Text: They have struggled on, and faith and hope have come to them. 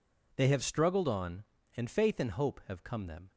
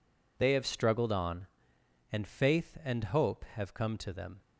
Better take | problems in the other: second | skips "to"; at 3.0 s

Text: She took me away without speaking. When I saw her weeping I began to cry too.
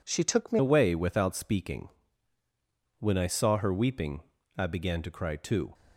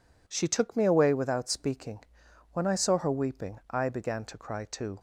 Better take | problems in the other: second | changes voice at "away"; from 0.5 s on; 5.2 s long // pauses between "weeping" and "I"; slight; at 4.2 s; 0.34 s long

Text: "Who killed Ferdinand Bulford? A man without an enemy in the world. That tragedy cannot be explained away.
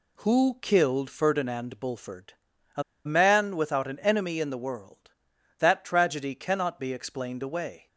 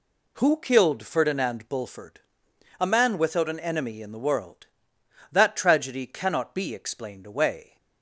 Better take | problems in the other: second | pauses between "A" and "man"; slight; at 2.8 s; 0.22 s long

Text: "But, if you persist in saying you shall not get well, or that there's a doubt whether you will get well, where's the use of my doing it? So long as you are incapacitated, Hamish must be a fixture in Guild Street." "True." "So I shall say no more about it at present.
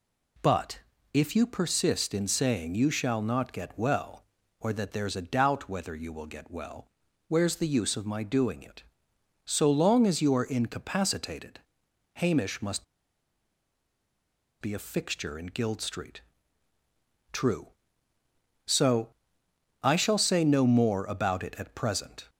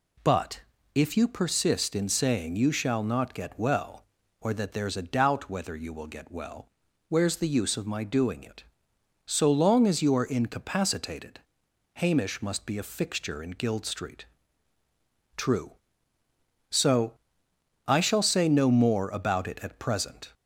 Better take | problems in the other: second | pauses between "must" and "be"; strong; at 12.8 s; 1.7 s long // pauses between "So" and "I"; noticeable; at 19.1 s; 0.68 s long; noticeable in the second

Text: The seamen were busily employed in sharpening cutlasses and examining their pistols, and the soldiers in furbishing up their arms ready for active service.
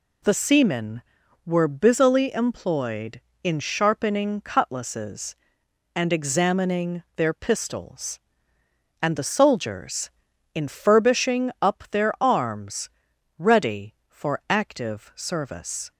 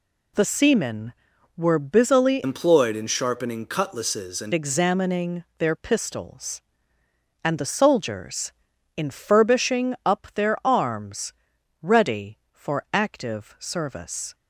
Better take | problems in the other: first | changes voice from "employed" to "and"; from 2.4 to 4.5 s; 2.1 s long // pauses between "arms" and "ready"; noticeable; at 11.3 s; 0.48 s long; noticeable in the first

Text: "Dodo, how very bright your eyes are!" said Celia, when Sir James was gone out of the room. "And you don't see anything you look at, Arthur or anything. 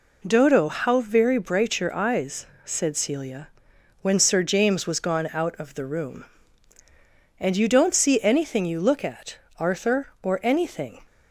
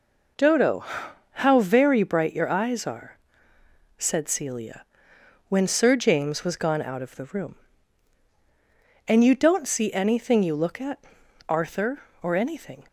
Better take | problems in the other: second | skips "are"; at 2.5 s

